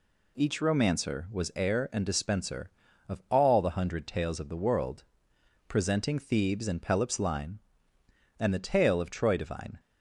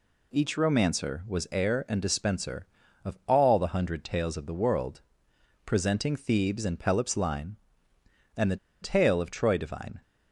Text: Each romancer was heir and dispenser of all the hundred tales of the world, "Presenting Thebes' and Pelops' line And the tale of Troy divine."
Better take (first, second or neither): first